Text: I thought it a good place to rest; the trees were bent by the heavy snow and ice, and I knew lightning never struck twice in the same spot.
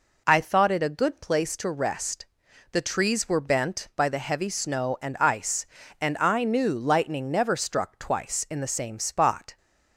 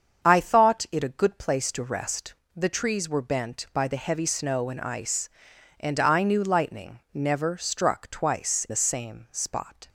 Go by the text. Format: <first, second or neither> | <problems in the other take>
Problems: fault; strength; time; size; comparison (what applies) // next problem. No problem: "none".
first | starts louder than the rest; strong; until 1.3 s; 7 dB // skips "in"; at 8.6 s